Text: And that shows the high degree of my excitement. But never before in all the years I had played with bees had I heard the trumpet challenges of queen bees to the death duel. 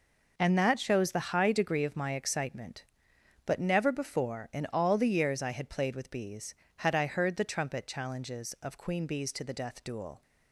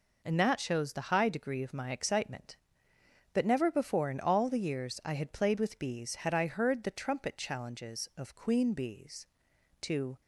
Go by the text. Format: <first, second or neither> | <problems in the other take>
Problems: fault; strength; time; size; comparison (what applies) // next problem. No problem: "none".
first | stops before "the death duel"; at 10.2 s